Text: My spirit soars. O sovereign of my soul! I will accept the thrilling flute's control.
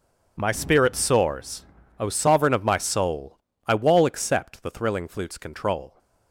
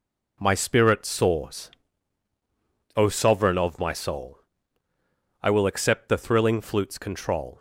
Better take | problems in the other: second | says "wall" for "will"; at 3.7 s

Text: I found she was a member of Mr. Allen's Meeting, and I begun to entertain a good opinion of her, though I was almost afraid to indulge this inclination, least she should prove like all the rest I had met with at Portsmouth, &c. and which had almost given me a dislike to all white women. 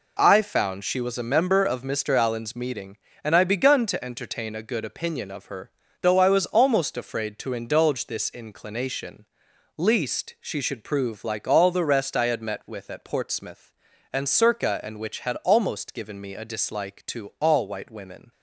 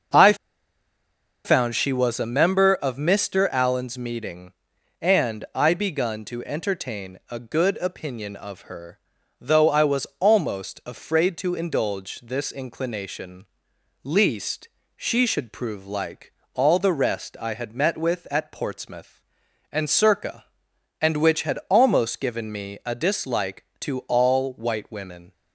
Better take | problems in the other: first | starts louder than the rest; noticeable; until 2.2 s; 6 dB // pauses between "I" and "found"; at 0.3 s; 1.1 s long // pauses between "least" and "she"; slight; at 14.6 s; 0.26 s long // pauses between "like" and "all"; slight; at 16.3 s; 0.22 s long

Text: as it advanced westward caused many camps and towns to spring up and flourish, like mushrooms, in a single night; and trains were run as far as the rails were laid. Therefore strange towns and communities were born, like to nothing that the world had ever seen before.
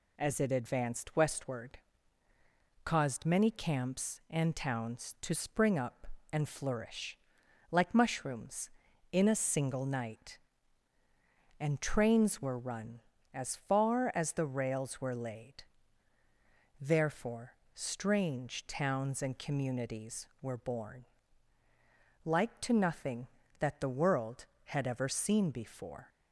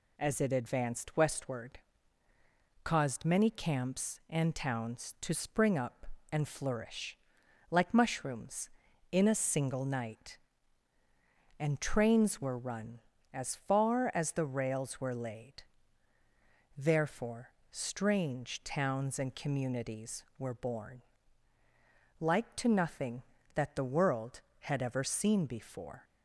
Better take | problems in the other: neither | pauses between "westward" and "caused"; the same in both // pauses between "Therefore" and "strange"; slight; the same in both

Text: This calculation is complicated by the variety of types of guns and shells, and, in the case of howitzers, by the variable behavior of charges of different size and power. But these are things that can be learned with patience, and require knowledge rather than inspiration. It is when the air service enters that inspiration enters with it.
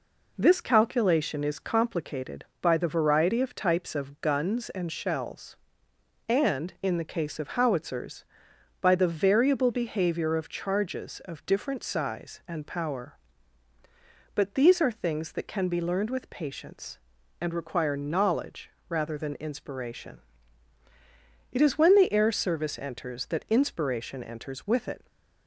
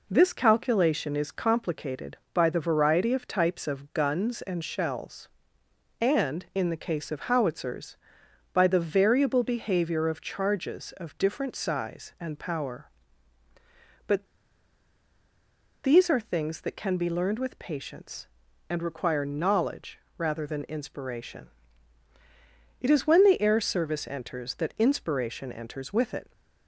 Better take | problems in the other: first | pauses between "But" and "these"; strong; at 14.2 s; 1.5 s long // pauses between "knowledge" and "rather"; slight; at 19.9 s; 0.18 s long; slight in the first

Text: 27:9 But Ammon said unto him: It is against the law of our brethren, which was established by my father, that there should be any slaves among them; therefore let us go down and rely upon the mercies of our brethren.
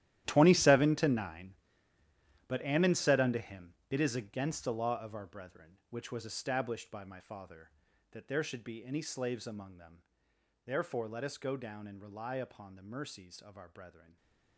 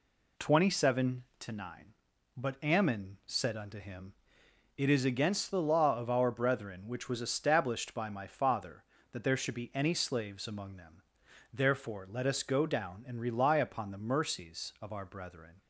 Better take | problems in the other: second | gets quieter; strong; throughout; 16.5 dB

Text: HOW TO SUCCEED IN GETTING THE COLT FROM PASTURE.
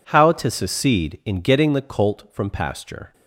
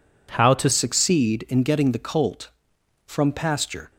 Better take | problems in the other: first | changes voice at "SUCCEED"; from 0.7 s on; 3.2 s long

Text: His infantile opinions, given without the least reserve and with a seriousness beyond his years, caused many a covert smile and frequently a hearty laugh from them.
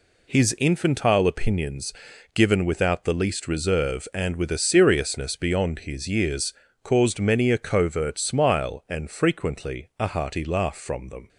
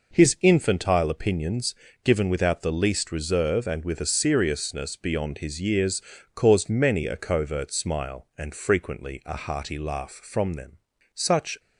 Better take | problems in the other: first | goes on to say "Such"; slight; from 11.1 s on; 0.46 s long

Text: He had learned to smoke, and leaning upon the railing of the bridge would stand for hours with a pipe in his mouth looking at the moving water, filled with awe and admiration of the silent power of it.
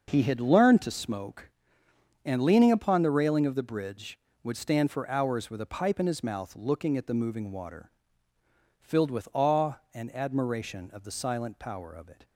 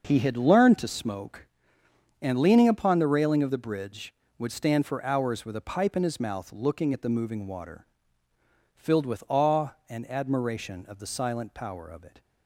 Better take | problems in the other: neither | starts louder than the rest; the same in both

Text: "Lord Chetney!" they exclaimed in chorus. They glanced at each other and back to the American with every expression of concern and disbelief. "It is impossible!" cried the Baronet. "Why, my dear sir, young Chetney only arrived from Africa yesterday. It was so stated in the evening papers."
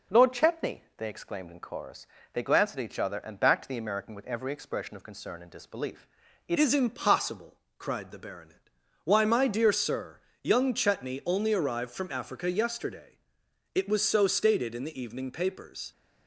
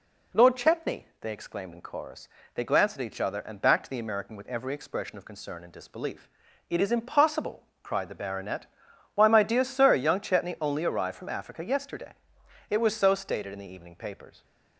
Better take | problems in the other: second | changes voice at "is"; from 6.5 s on; 9.4 s long

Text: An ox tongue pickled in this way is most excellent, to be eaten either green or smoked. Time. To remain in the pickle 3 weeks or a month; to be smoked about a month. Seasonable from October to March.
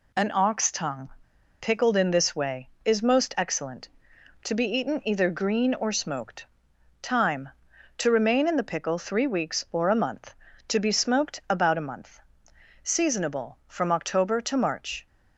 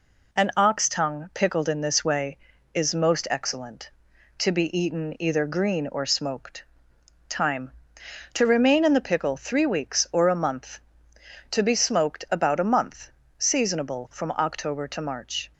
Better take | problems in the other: second | pauses between "tongue" and "pickled"; noticeable; at 1.0 s; 0.51 s long

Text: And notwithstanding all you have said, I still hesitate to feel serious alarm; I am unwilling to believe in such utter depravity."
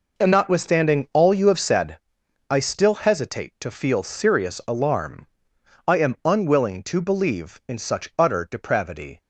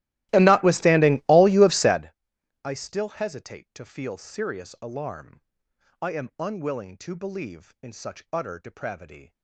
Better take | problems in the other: first | starts louder than the rest; strong; until 2.1 s; 15.5 dB

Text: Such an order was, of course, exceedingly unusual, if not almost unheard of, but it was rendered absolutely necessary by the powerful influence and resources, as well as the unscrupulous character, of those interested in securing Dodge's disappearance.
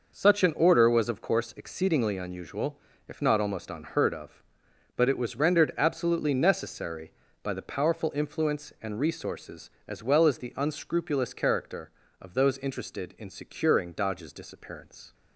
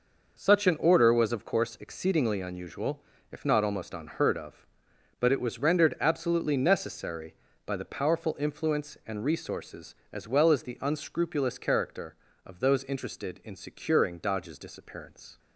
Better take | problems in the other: neither | none

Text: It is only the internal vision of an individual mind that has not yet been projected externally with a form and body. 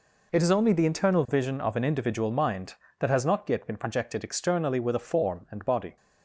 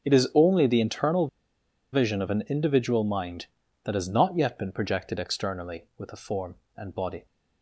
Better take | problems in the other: first | pauses between "internal" and "vision"; noticeable; at 1.2 s; 0.65 s long

